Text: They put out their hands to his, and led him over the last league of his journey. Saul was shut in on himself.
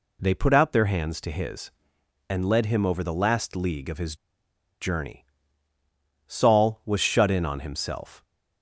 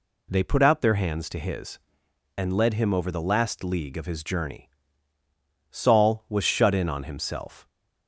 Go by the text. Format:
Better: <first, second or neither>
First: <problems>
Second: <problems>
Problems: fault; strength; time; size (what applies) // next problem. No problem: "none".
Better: second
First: pauses between "his" and "journey"; noticeable; at 4.1 s; 0.66 s long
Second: none